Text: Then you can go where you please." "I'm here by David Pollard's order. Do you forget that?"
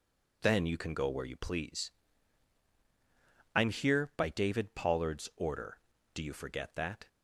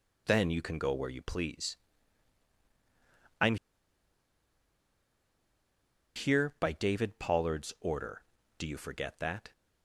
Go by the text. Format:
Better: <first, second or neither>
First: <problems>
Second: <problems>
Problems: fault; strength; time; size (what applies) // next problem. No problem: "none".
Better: first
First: none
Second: pauses between "I'm" and "here"; strong; at 3.5 s; 2.5 s long